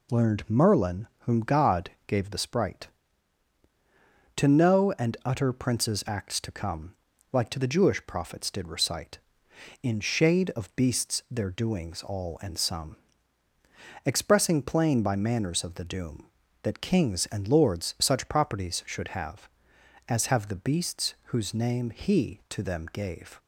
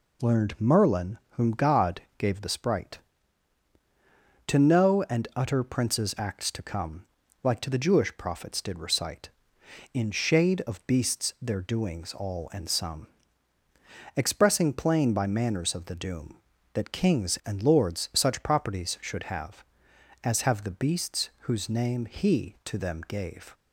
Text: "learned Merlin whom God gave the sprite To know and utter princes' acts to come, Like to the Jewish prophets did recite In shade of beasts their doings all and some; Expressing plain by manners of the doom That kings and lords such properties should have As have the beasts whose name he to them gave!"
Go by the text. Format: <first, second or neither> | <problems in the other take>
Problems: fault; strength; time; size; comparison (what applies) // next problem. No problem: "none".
neither | pauses between "God" and "gave"; slight; the same in both